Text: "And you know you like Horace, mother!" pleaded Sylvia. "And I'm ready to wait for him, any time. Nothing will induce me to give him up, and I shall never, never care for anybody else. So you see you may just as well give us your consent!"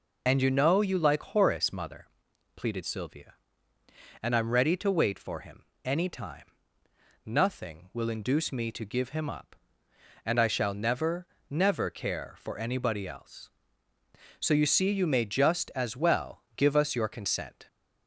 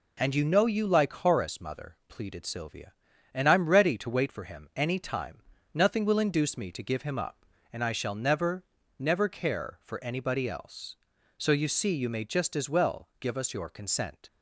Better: second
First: loses the start of "And"; at 0.2 s; 40 ms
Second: none

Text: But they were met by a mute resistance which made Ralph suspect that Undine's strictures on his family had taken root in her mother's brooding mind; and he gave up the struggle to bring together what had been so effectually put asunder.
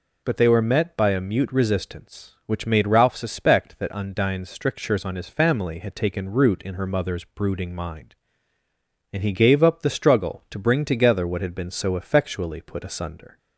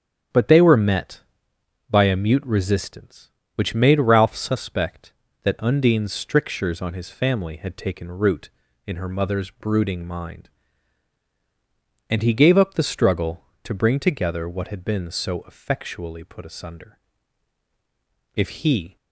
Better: first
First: none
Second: starts louder than the rest; strong; until 2.0 s; 9 dB // goes on to say "If he"; noticeable; from 18.3 s on; 0.62 s long

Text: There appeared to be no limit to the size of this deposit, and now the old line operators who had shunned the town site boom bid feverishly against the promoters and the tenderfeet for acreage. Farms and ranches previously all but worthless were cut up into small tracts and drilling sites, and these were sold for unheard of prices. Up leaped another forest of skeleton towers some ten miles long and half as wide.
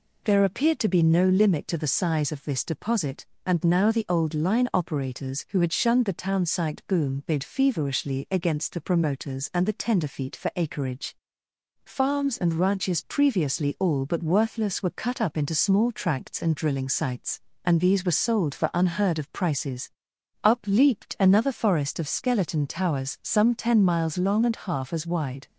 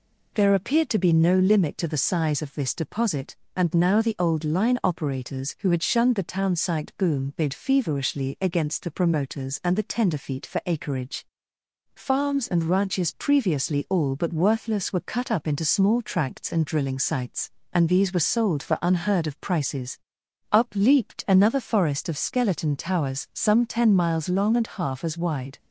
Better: neither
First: none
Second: none

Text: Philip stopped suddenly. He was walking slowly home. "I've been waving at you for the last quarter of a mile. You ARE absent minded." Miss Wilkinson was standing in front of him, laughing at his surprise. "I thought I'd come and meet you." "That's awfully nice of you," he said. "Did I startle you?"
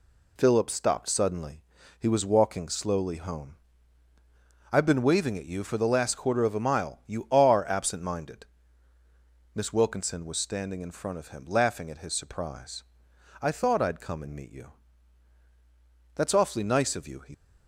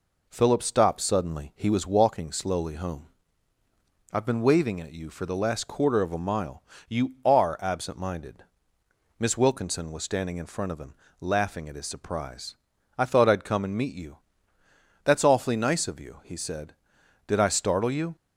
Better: second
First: stops before "said Did I startle you"; at 17.3 s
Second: none

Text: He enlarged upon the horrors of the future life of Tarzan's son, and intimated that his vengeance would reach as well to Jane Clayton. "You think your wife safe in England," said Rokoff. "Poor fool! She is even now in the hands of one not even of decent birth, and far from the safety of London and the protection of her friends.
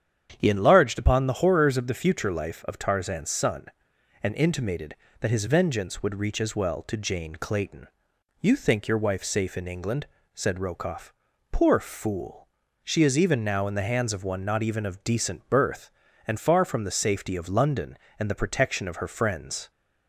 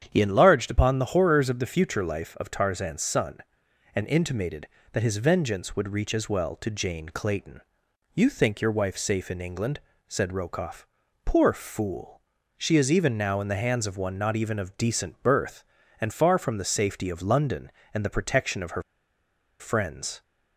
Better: first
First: starts louder than the rest; strong; until 1.3 s; 8.5 dB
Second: starts louder than the rest; strong; until 1.0 s; 8.5 dB // pauses between "her" and "friends"; noticeable; at 18.8 s; 0.77 s long

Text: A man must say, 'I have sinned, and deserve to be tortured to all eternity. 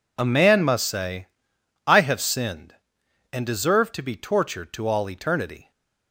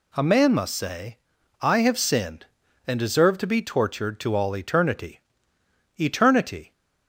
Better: first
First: none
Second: says "eternity" twice; at 6.0 s

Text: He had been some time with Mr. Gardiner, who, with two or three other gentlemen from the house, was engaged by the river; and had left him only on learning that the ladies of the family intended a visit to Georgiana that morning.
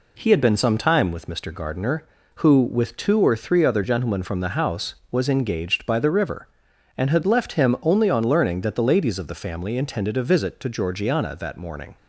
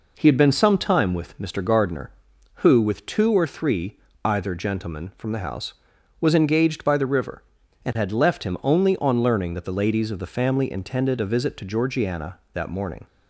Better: first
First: none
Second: says "either" for "other"; at 4.2 s

